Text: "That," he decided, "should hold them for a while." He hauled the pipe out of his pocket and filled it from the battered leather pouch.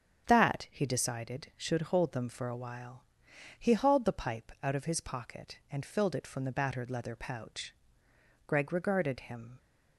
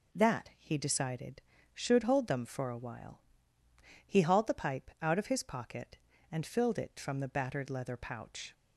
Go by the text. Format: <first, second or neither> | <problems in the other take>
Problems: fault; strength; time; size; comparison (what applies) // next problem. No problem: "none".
second | starts louder than the rest; strong; until 1.3 s; 7.5 dB // goes on to say "Greg regarded him"; noticeable; from 8.4 s on; 1.1 s long